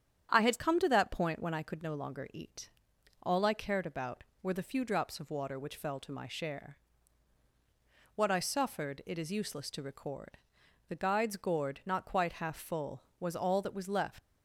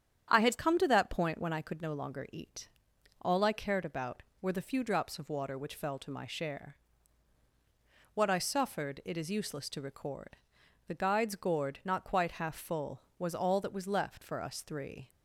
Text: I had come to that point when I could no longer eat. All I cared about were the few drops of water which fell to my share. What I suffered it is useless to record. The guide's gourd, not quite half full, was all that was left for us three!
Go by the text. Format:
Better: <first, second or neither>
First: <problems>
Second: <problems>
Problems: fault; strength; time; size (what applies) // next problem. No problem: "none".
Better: second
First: starts louder than the rest; strong; until 1.3 s; 9 dB // stops before "for us three"; at 14.2 s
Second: starts louder than the rest; strong; until 1.3 s; 9 dB